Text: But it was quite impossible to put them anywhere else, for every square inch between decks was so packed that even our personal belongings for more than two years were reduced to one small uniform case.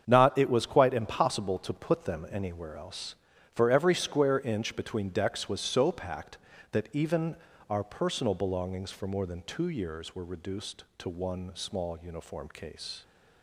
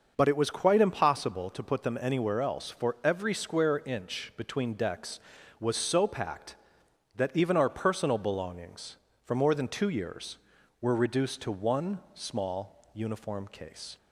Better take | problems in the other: second | starts louder than the rest; strong; until 1.0 s; 7.5 dB; noticeable in the second // says "Not" for "But"; at 0.0 s // pauses between "even" and "our"; slight; at 7.3 s; 0.34 s long

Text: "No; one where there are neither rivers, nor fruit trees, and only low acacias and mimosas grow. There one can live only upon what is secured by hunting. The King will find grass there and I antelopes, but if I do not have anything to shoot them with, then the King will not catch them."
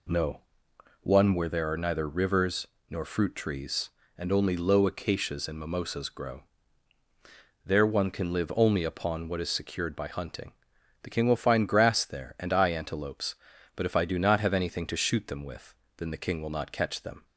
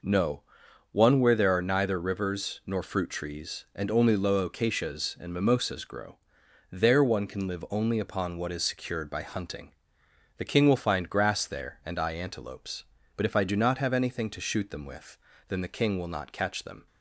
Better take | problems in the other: neither | none

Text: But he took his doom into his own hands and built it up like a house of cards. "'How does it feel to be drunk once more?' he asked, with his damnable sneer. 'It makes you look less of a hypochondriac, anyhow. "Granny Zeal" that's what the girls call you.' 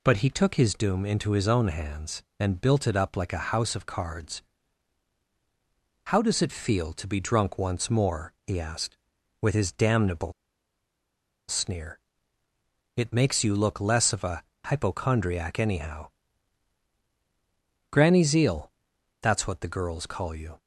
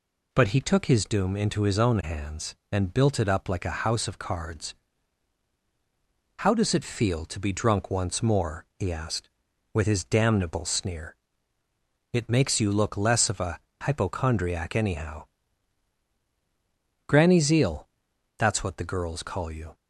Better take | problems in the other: second | pauses between "damnable" and "sneer"; at 10.3 s; 1.1 s long // pauses between "a" and "hypochondriac"; slight; at 14.4 s; 0.24 s long; slight in the second // pauses between "Zeal" and "that's"; noticeable; at 18.7 s; 0.52 s long; noticeable in the second

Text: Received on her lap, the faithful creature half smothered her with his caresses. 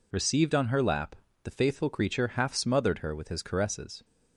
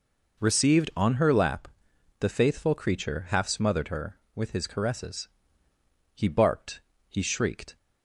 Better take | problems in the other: first | goes on to say "He barked he shrieked"; from 6.1 s on; 1.6 s long

